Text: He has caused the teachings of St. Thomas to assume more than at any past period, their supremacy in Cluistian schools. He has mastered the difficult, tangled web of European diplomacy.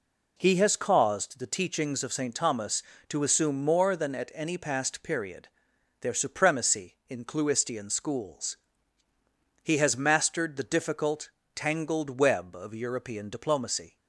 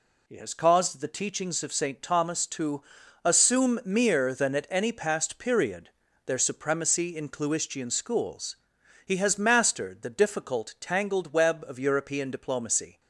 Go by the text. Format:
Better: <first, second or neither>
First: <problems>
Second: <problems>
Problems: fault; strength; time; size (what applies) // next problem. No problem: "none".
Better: first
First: none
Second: pauses between "to" and "assume"; at 2.8 s; 0.42 s long // says "mere" for "more"; at 3.8 s